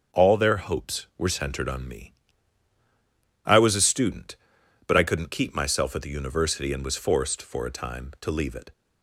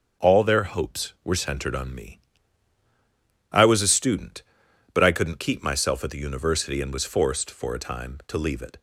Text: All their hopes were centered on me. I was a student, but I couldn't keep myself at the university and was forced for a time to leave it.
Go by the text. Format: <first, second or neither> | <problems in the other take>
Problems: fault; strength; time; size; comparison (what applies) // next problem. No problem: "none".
neither | starts louder than the rest; the same in both